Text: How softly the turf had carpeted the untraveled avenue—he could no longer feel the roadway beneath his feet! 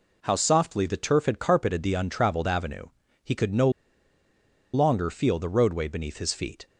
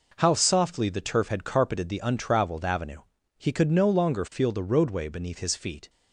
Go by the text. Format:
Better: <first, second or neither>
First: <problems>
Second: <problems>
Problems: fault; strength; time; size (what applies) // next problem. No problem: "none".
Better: second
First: pauses between "no" and "longer"; at 3.7 s; 1.0 s long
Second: none